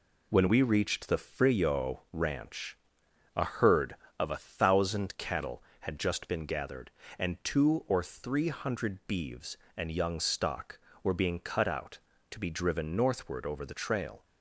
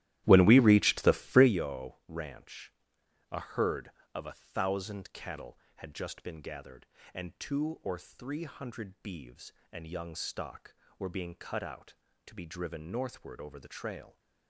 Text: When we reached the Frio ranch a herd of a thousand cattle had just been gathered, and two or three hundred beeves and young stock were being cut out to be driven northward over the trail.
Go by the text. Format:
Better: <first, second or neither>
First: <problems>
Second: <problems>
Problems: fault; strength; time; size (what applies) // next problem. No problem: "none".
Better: first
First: pauses between "ranch" and "a"; noticeable; at 2.7 s; 0.60 s long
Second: starts louder than the rest; strong; until 1.6 s; 14.5 dB // pauses between "ranch" and "a"; noticeable; at 2.7 s; 0.60 s long